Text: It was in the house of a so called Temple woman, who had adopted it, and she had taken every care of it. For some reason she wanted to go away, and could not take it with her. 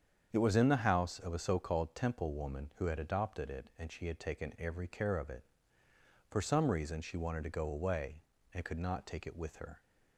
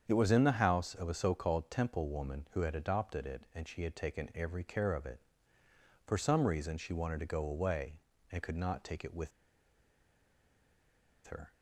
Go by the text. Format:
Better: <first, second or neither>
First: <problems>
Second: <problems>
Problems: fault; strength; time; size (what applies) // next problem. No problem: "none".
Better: first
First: starts louder than the rest; strong; until 1.3 s; 7.5 dB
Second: starts louder than the rest; strong; until 1.0 s; 7.5 dB // pauses between "with" and "her"; strong; at 9.3 s; 1.9 s long